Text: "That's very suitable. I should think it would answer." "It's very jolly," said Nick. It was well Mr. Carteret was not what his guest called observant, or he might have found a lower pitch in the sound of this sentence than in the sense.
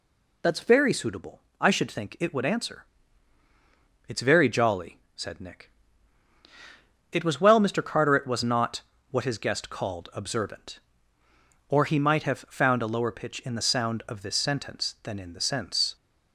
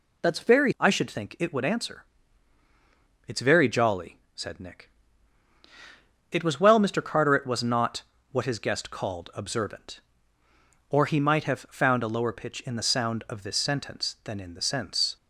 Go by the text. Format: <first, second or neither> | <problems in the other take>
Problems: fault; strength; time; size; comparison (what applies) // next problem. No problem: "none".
first | skips "suitable"; at 0.7 s // pauses between "not" and "what"; slight; at 8.0 s; 0.28 s long; slight in the first